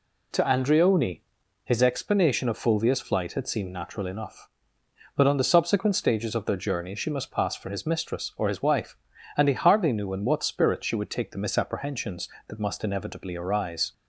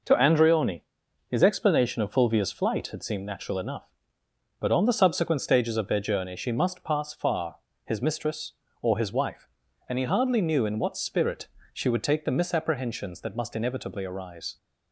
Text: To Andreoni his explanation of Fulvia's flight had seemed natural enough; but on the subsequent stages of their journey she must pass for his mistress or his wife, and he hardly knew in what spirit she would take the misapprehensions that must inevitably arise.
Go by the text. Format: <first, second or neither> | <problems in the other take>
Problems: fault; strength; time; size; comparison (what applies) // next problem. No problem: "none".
first | pauses between "Andreoni" and "his"; noticeable; at 0.8 s; 0.46 s long; also in the first // says "far" for "for"; at 7.1 s // pauses between "spirit" and "she"; slight; at 11.4 s; 0.22 s long